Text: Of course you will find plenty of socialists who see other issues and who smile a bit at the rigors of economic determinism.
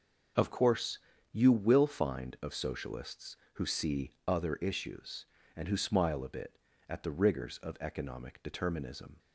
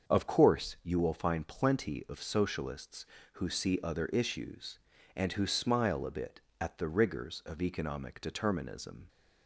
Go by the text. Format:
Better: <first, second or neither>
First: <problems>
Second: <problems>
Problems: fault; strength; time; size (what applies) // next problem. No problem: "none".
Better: second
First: starts louder than the rest; until 1.7 s; 6 dB // pauses between "course" and "you"; slight; at 0.9 s; 0.34 s long // skips "plenty"; at 2.3 s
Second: starts louder than the rest; until 1.1 s; 6.5 dB